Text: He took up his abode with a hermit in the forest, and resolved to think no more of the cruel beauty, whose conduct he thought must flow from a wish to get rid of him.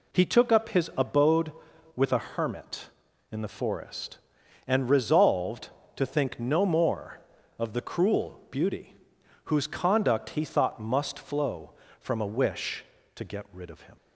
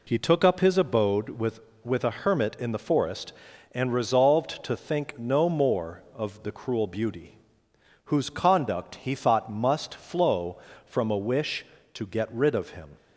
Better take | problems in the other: first | says "with" twice; at 1.8 s

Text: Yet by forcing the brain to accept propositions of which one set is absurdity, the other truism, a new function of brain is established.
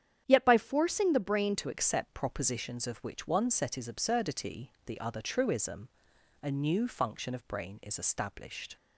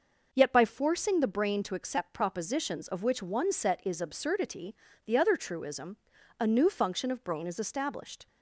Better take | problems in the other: second | starts louder than the rest; strong; until 1.2 s; 9 dB // changes voice at "to"; from 1.5 s on; 7.2 s long

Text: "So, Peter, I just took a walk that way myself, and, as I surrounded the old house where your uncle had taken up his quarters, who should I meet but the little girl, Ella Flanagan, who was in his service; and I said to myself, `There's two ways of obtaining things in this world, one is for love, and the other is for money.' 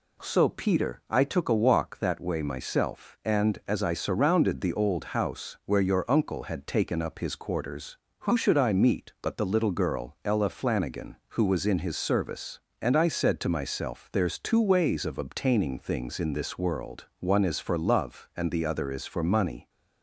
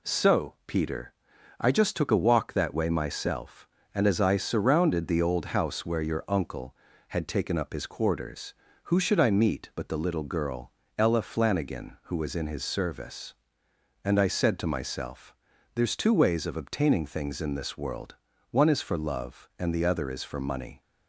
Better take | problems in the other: second | skips "just"; at 1.2 s

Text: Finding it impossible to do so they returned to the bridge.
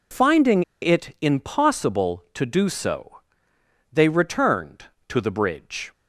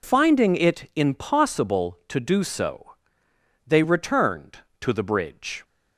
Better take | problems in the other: second | pauses between "Finding" and "it"; slight; at 0.6 s; 0.20 s long // pauses between "so" and "they"; noticeable; at 3.1 s; 0.74 s long; noticeable in the second

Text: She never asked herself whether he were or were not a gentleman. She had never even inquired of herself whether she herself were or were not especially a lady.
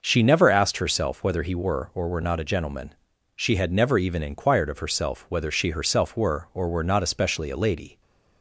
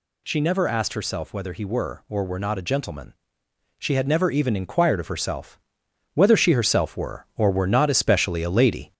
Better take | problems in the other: first | gets louder; slight; throughout; 2.5 dB // pauses between "herself" and "whether"; noticeable; at 5.5 s; 0.56 s long

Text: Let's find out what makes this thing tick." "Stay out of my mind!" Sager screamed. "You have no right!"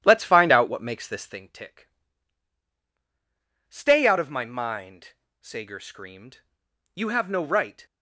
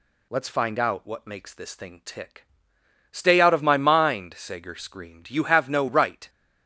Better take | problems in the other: second | starts louder than the rest; strong; until 1.4 s; 11.5 dB

